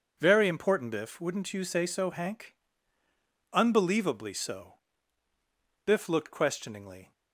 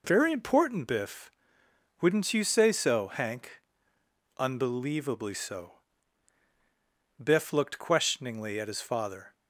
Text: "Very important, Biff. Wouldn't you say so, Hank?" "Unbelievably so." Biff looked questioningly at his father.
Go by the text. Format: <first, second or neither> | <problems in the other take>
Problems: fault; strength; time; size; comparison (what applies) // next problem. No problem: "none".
second | stops before "at his father"; at 7.1 s